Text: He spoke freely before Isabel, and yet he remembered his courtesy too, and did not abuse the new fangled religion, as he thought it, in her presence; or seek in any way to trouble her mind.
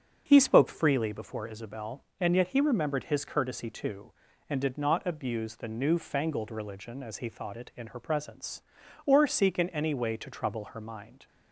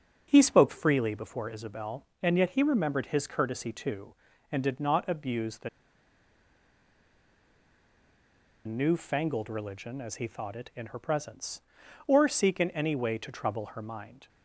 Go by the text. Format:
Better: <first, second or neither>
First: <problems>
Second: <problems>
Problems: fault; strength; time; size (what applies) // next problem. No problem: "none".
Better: first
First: starts louder than the rest; until 1.2 s; 7 dB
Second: starts louder than the rest; until 1.3 s; 7 dB // pauses between "the" and "new"; strong; at 5.6 s; 2.9 s long